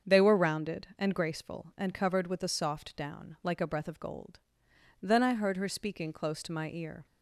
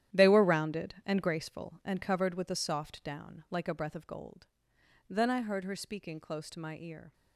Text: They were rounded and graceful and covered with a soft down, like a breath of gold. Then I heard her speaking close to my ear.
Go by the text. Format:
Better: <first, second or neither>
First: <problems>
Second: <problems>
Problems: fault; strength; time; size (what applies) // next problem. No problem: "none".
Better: first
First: starts louder than the rest; strong; until 1.1 s; 7 dB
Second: gets quieter; strong; throughout; 12 dB // starts louder than the rest; strong; until 1.2 s; 11.5 dB